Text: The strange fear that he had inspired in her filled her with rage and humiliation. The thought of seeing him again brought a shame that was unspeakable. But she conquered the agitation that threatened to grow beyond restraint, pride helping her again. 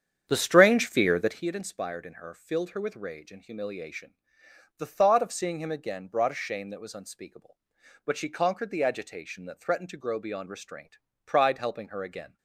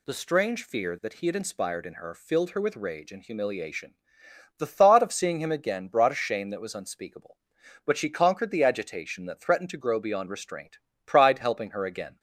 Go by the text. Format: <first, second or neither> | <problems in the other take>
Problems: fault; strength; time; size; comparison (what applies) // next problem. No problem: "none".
second | starts louder than the rest; strong; until 1.5 s; 8.5 dB